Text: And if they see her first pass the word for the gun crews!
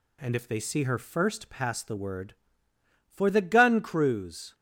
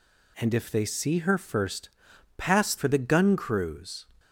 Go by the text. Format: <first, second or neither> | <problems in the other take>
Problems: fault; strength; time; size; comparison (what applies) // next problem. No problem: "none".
first | pauses between "first" and "pass"; noticeable; at 1.8 s; 0.48 s long // skips "the word"; at 2.7 s